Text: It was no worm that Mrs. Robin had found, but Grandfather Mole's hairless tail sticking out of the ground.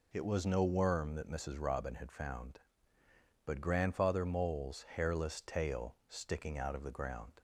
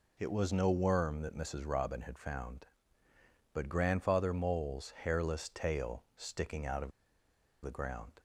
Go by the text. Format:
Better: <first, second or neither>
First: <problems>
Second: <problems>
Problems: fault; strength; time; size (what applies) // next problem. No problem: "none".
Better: first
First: none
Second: pauses between "of" and "the"; noticeable; at 6.9 s; 0.73 s long